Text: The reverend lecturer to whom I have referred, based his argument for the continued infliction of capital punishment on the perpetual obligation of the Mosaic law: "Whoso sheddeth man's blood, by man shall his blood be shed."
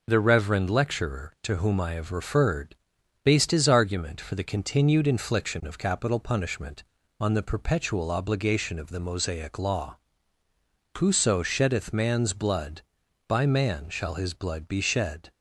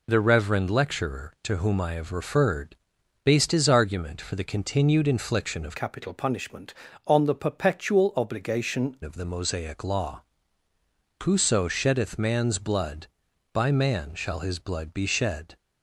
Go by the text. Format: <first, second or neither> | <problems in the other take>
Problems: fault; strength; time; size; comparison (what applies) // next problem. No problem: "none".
first | changes voice from "capital" to "obligation"; from 5.7 to 8.9 s; 3.2 s long